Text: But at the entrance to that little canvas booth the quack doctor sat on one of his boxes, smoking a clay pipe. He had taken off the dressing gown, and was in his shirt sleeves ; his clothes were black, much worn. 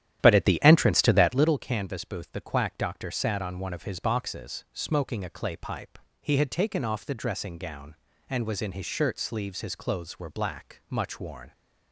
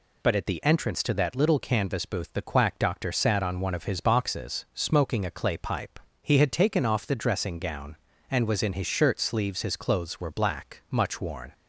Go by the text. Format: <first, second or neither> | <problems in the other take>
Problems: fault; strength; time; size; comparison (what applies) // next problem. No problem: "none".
second | starts louder than the rest; strong; until 1.6 s; 11 dB